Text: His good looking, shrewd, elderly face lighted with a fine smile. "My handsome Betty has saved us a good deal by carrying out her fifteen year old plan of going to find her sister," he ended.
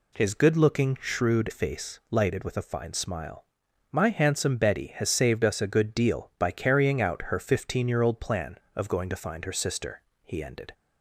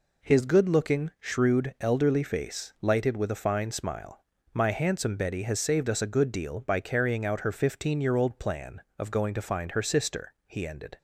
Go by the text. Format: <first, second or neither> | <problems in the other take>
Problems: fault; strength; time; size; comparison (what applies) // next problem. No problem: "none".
second | skips "elderly"; at 1.4 s